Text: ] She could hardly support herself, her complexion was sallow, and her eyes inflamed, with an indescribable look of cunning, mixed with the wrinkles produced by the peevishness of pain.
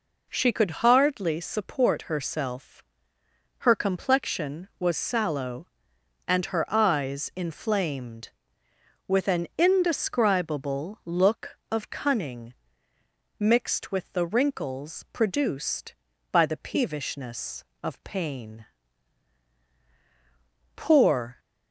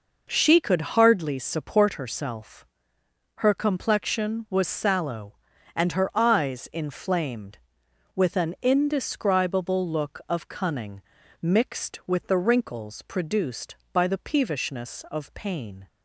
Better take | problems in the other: second | goes on to say "Poor"; noticeable; from 20.7 s on; 0.64 s long

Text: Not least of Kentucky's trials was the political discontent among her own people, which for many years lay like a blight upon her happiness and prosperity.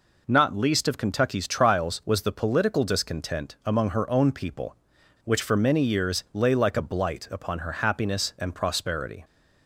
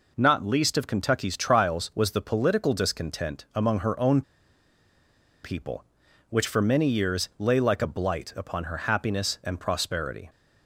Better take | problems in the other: first | pauses between "own" and "people"; at 4.2 s; 1.2 s long

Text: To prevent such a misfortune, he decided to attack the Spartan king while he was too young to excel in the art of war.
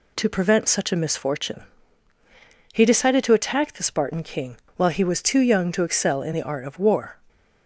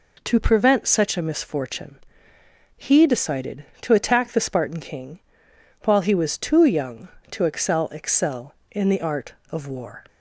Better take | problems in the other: first | pauses between "king" and "while"; noticeable; at 5.2 s; 0.64 s long; slight in the first // says "excel" twice; at 7.8 s

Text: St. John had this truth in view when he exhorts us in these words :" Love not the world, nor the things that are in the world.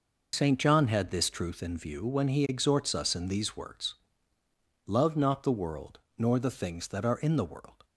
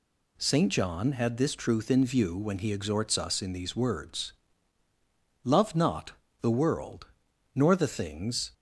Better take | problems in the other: first | pauses between "not" and "the"; slight; at 6.1 s; 0.26 s long // stops before "that are in the world"; at 8.5 s

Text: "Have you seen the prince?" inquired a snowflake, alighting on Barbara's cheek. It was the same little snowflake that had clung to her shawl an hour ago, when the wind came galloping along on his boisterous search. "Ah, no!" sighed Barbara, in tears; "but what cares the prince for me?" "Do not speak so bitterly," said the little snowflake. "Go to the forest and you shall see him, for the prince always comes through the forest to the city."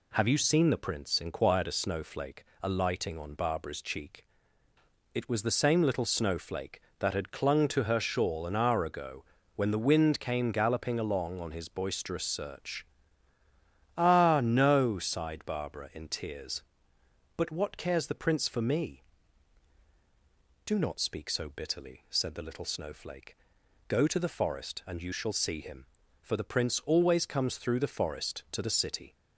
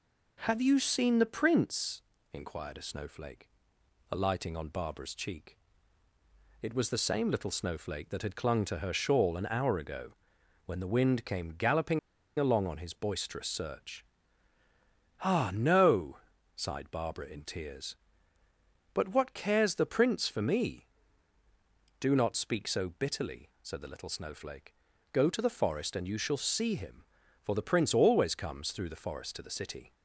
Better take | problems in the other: first | pauses between "galloping" and "along"; at 11.9 s; 0.39 s long

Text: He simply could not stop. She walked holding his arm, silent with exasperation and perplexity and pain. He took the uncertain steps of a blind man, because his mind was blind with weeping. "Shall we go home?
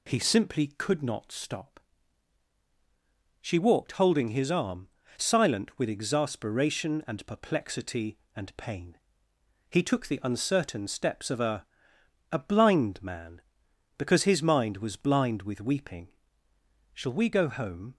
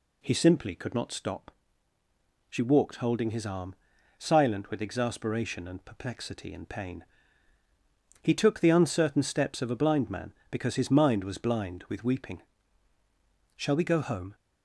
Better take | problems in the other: second | says "a" twice; at 12.3 s

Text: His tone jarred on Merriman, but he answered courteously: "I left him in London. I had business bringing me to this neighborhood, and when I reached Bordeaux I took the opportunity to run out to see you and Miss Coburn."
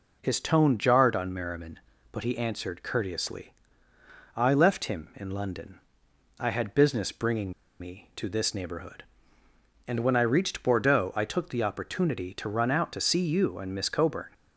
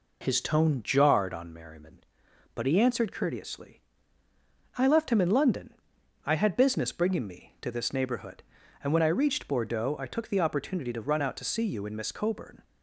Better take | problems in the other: second | pauses between "bringing" and "me"; slight; at 7.5 s; 0.27 s long

